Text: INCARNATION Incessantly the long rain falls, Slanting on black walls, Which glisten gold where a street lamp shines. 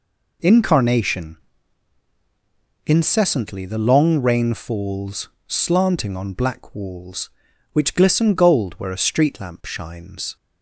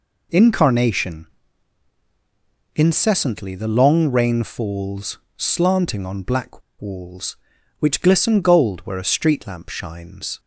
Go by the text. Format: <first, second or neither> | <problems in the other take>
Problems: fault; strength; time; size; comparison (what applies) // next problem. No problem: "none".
first | pauses between "INCARNATION" and "Incessantly"; strong; at 1.2 s; 1.5 s long; strong in the first // pauses between "black" and "walls"; slight; at 6.6 s; 0.20 s long